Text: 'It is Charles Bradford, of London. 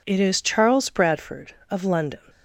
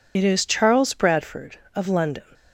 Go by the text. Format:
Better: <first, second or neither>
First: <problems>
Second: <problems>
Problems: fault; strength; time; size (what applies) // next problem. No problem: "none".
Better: first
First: none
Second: loses the start of "It"; at 0.1 s; 60 ms